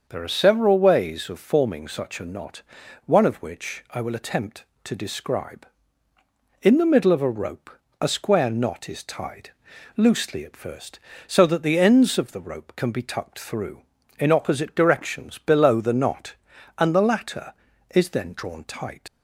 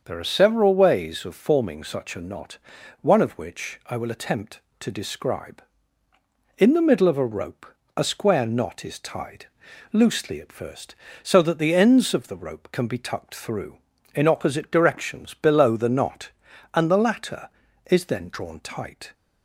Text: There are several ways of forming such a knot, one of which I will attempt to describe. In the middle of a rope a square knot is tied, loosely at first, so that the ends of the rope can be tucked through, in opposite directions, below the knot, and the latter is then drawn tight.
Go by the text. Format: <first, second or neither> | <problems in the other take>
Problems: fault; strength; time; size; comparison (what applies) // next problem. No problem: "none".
second | starts louder than the rest; until 1.0 s; 6.5 dB; also in the second // pauses between "rope" and "a"; slight; at 7.7 s; 0.28 s long; slight in the second // leaves "tight" unfinished; at 19.0 s; 95 ms